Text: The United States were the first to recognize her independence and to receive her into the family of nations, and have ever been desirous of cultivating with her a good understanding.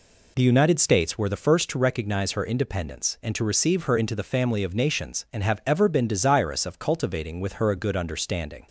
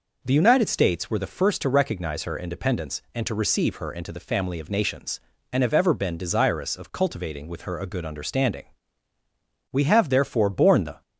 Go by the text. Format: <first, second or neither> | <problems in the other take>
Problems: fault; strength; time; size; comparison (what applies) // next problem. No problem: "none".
first | goes on to say "We have therefore borne the"; noticeable; from 9.7 s on; 1.3 s long